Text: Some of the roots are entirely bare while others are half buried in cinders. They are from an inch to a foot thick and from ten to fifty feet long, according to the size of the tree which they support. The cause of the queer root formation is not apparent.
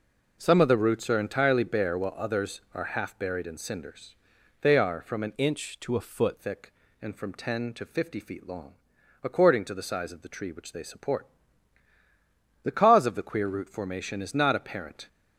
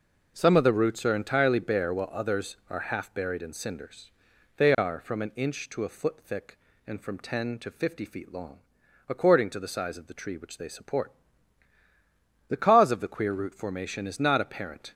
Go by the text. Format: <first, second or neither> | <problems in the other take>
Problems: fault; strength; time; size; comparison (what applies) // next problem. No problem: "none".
second | changes voice from "inch" to "foot"; from 5.3 to 6.3 s; 1.0 s long